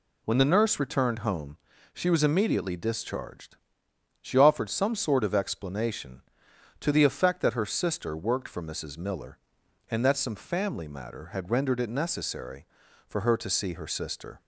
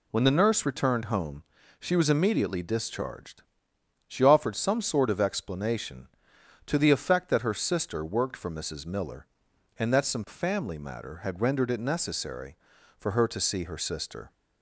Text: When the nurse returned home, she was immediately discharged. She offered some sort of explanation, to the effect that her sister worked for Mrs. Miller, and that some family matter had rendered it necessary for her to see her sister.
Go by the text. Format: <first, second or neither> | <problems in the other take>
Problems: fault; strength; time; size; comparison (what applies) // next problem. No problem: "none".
neither | none